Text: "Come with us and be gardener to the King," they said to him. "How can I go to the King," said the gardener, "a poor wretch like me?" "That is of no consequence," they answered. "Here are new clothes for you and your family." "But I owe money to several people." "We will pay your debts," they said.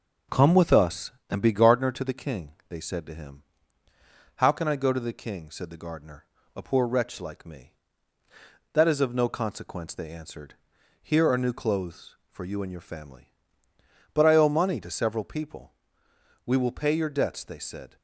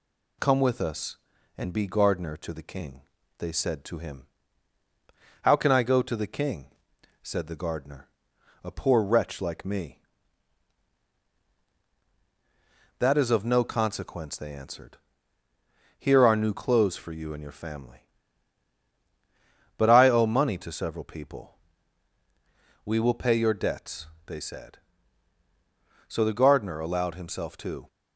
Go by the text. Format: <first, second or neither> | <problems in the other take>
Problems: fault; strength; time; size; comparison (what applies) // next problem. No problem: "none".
first | goes on to say "So the gardener allowed himself to"; strong; from 26.0 s on; 1.8 s long